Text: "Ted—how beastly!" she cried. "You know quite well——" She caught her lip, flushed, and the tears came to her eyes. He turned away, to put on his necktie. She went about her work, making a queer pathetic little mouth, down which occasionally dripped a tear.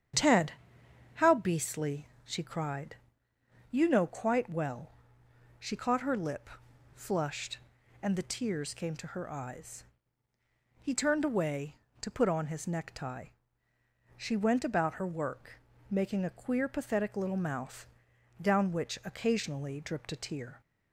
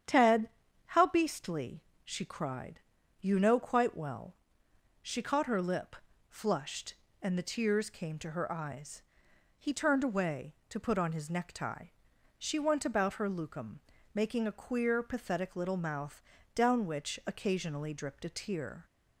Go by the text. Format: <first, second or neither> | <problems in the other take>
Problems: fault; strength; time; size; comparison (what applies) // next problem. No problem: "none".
first | starts louder than the rest; strong; until 1.4 s; 9 dB; strong in the first // says "lucum" for "work"; at 13.2 s